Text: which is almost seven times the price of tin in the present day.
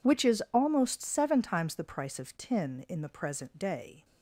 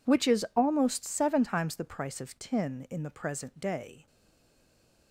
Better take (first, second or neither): first